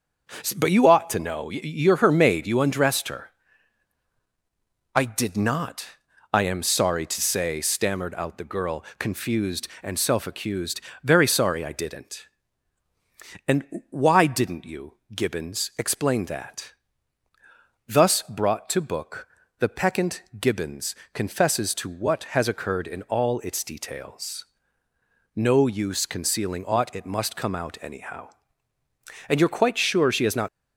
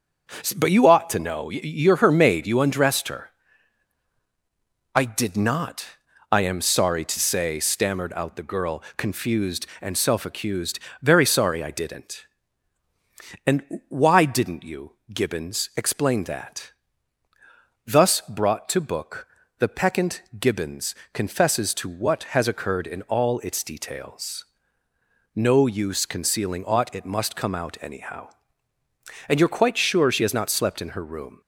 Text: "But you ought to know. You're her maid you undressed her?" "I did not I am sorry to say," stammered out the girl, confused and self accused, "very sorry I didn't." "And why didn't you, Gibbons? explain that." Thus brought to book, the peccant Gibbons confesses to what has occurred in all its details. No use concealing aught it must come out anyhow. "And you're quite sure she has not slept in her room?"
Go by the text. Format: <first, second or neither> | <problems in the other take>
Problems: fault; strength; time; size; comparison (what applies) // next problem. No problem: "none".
second | pauses between "not" and "I"; noticeable; at 5.8 s; 0.48 s long; noticeable in the second // pauses between "peccant" and "Gibbons"; slight; at 20.2 s; 0.18 s long; slight in the second // pauses between "Gibbons" and "confesses"; slight; at 20.9 s; 0.16 s long; slight in the second // stops before "slept in her room"; at 30.4 s